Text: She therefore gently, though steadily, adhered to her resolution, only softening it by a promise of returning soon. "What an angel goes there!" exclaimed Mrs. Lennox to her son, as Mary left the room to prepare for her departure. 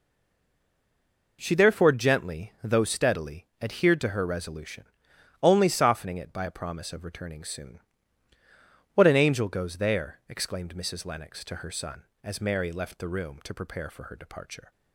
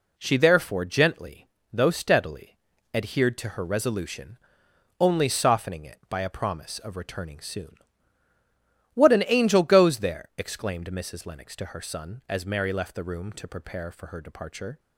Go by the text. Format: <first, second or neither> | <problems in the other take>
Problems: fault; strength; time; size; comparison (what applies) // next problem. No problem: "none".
second | stays silent before the first word; noticeable; until 1.3 s; 1.3 s long